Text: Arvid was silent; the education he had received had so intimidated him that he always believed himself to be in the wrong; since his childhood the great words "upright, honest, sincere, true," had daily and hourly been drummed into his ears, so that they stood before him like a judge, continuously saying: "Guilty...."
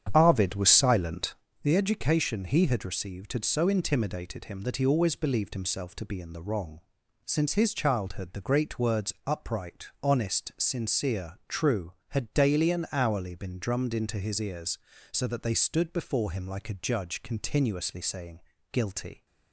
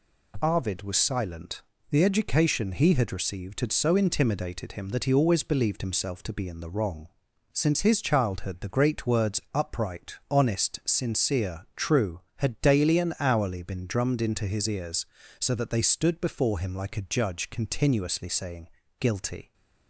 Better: second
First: starts louder than the rest; strong; until 1.5 s; 8.5 dB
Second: none

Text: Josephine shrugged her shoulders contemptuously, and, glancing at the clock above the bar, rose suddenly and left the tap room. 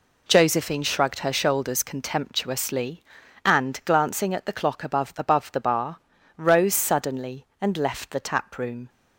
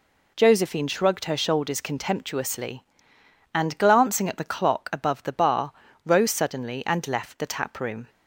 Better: second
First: says "above" twice; at 5.1 s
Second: none

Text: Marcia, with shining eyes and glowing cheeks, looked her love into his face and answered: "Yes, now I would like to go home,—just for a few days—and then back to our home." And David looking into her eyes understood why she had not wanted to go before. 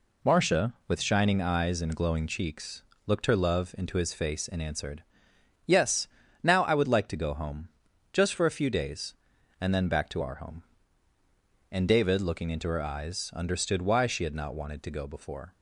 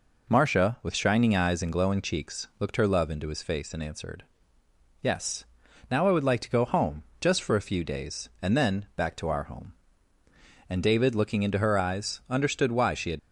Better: first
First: none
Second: stops before "not wanted to go before"; at 13.1 s

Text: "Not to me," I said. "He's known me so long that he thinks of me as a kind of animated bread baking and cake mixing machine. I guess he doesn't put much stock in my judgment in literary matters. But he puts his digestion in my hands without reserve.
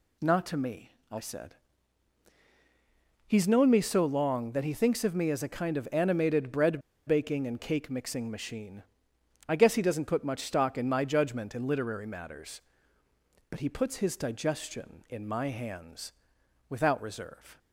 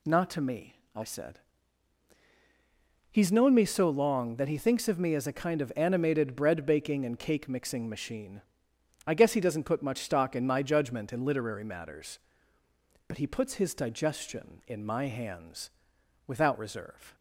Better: second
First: pauses between "bread" and "baking"; slight; at 6.8 s; 0.27 s long // pauses between "hands" and "without"; noticeable; at 16.1 s; 0.56 s long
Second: pauses between "hands" and "without"; noticeable; at 15.6 s; 0.56 s long

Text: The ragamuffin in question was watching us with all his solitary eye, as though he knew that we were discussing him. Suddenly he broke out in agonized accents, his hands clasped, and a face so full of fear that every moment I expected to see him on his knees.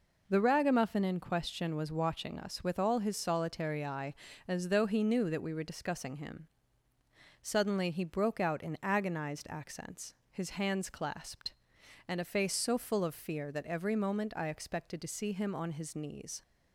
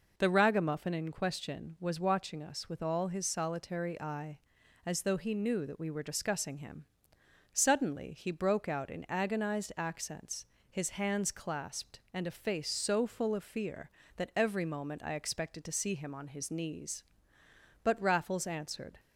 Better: first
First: none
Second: goes on to say "But Raffles answered"; noticeable; from 17.8 s on; 1.1 s long

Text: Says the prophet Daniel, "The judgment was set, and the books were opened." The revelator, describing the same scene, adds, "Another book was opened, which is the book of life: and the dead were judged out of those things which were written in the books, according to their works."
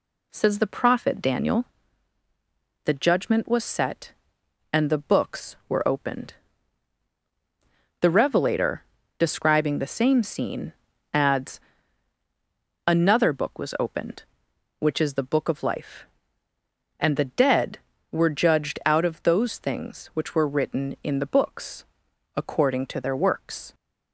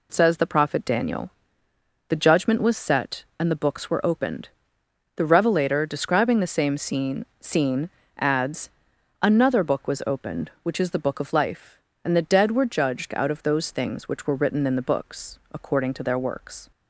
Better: first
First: none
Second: says "scene" twice; at 7.3 s

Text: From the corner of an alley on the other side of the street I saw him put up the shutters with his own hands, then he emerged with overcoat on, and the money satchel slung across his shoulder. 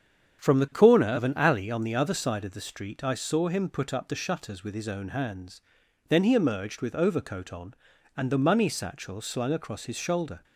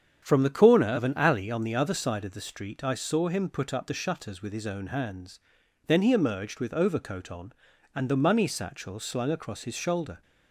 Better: neither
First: starts louder than the rest; strong; until 1.4 s; 8 dB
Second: starts louder than the rest; strong; until 1.2 s; 8 dB

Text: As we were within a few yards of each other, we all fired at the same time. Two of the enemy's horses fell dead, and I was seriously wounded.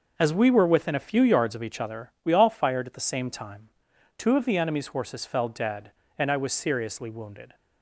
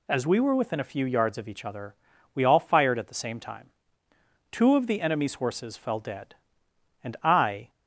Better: first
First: none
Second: stops before "was seriously wounded"; at 7.6 s

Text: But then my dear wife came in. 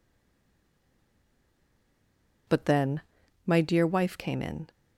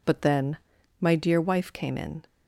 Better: second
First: stays silent before the first word; until 2.4 s; 2.4 s long // pauses between "then" and "my"; at 3.0 s; 0.44 s long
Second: pauses between "then" and "my"; at 0.5 s; 0.42 s long

